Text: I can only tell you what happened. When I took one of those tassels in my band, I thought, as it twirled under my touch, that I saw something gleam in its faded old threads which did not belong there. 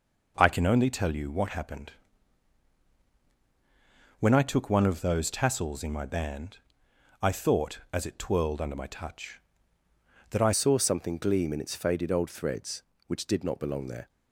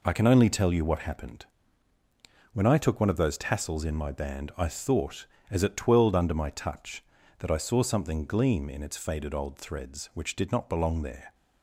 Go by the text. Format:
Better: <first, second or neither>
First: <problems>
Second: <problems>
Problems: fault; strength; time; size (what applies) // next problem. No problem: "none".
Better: second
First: changes voice at "saw"; from 10.5 s on; 3.5 s long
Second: none